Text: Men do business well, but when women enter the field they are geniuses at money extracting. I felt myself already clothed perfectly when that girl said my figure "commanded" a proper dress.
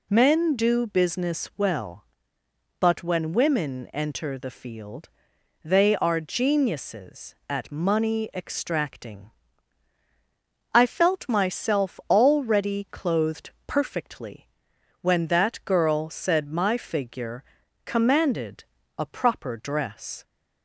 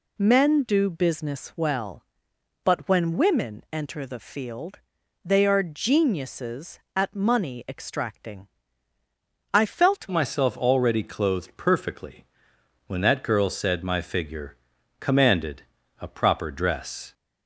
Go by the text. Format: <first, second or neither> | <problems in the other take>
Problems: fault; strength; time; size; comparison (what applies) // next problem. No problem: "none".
first | pauses between "field" and "they"; noticeable; at 4.7 s; 0.46 s long; noticeable in the first // changes voice at "myself"; from 10.1 s on; 7.0 s long // pauses between "perfectly" and "when"; noticeable; at 12.2 s; 0.64 s long; noticeable in the first // pauses between "figure" and "commanded"; at 14.5 s; 0.42 s long; also in the first // pauses between "commanded" and "a"; at 15.6 s; 0.40 s long; slight in the first